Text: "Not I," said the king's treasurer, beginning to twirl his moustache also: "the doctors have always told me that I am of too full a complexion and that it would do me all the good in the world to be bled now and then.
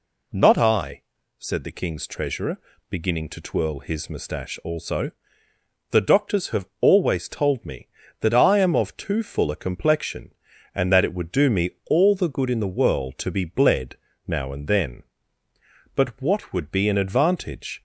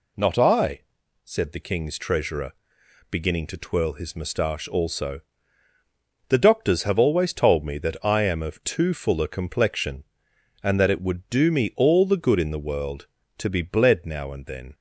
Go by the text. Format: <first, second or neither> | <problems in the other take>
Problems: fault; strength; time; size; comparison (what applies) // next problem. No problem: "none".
second | pauses between "bled" and "now"; slight; at 13.9 s; 0.32 s long // goes on to say "But what would be an advantage"; strong; from 15.9 s on; 1.8 s long